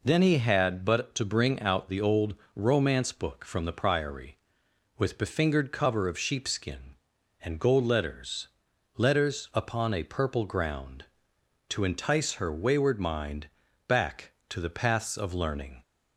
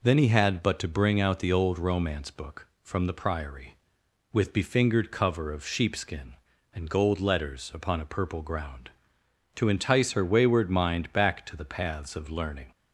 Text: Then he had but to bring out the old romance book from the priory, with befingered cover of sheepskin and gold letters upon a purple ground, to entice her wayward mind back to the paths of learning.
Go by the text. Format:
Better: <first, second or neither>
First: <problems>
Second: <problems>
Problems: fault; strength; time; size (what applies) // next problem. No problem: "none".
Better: second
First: pauses between "old" and "romance"; slight; at 2.3 s; 0.22 s long // says "letters" twice; at 8.9 s // pauses between "mind" and "back"; at 13.4 s; 0.40 s long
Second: none